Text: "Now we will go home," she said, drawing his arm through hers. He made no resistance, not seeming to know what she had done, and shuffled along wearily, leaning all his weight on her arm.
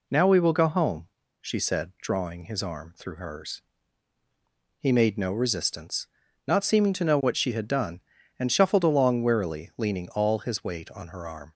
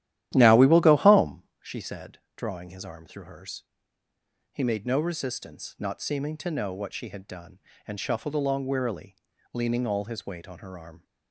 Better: first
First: none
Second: starts louder than the rest; strong; until 1.4 s; 12.5 dB

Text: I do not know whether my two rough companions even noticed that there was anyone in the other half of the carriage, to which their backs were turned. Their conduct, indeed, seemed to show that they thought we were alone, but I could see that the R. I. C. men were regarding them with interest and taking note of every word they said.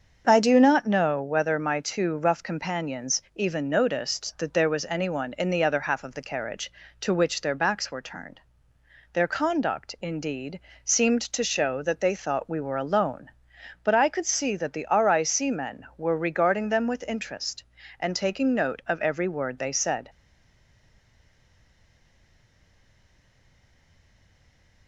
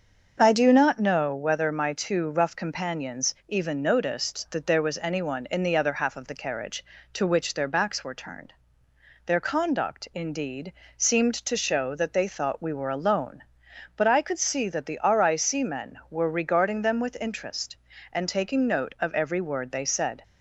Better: second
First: starts louder than the rest; until 1.2 s; 6.5 dB // stays silent after the last word; strong; from 20.0 s on; 4.8 s long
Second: starts louder than the rest; until 1.4 s; 6.5 dB

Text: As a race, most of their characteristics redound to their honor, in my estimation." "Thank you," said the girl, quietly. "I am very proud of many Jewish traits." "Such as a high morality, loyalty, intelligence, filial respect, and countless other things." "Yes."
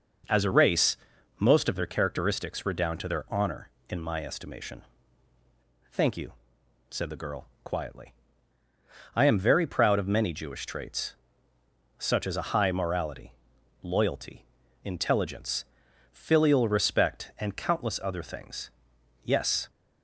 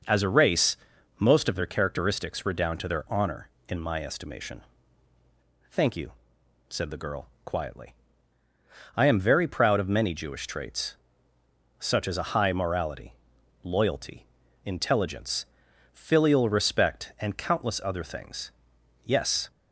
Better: neither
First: none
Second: none

